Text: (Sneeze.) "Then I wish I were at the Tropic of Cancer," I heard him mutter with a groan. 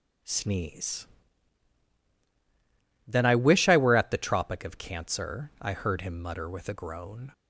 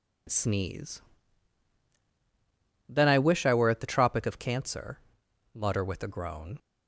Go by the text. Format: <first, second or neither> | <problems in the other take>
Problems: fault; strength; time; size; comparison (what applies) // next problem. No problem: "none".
first | skips "I heard him"; at 5.2 s